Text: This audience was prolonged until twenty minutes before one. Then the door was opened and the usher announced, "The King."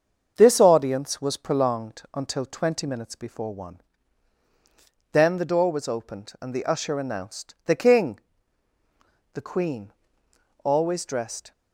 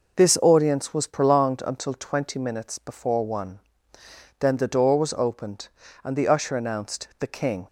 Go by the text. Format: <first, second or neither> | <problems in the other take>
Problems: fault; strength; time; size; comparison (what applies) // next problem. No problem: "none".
second | starts louder than the rest; until 1.3 s; 7 dB // goes on to say "The Queen always dressed"; strong; from 9.3 s on; 2.1 s long